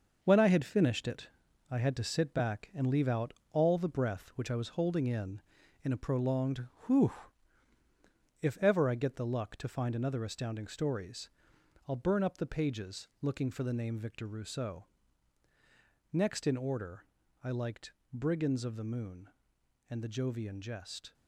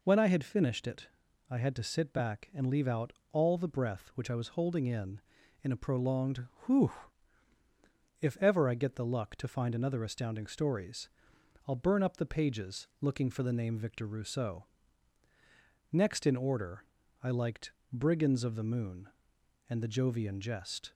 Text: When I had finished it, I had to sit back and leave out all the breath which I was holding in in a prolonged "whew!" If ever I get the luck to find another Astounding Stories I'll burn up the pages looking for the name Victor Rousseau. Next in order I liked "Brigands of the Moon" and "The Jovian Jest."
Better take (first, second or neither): second